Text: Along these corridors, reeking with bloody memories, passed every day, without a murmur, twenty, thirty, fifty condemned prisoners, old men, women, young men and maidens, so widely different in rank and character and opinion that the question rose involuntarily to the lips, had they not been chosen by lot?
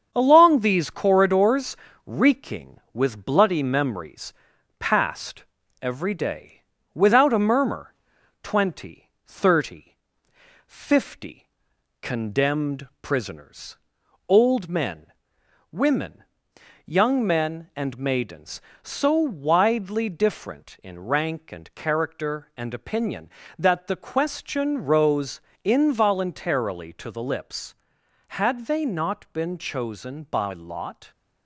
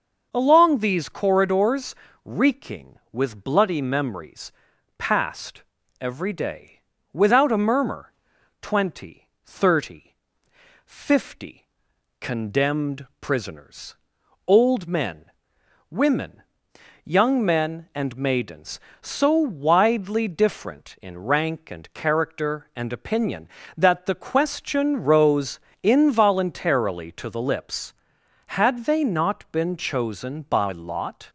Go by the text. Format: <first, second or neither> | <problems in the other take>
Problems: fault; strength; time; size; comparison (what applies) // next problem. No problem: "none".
second | gets quieter; slight; throughout; 3.5 dB // starts louder than the rest; strong; until 1.1 s; 7 dB; noticeable in the second // pauses between "passed" and "every"; slight; at 5.4 s; 0.36 s long; slight in the second // pauses between "fifty" and "condemned"; noticeable; at 11.4 s; 0.54 s long; noticeable in the second // pauses between "rose" and "involuntarily"; slight; at 25.3 s; 0.24 s long; slight in the second